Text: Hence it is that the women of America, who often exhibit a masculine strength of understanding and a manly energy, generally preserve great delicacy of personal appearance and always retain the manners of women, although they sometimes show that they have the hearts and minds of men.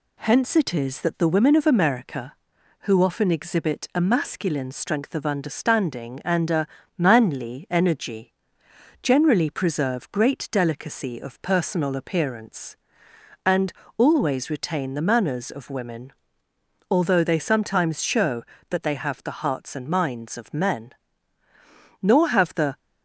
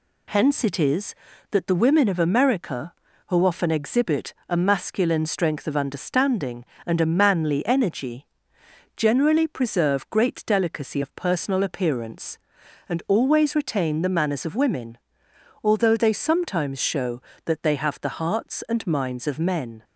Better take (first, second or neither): second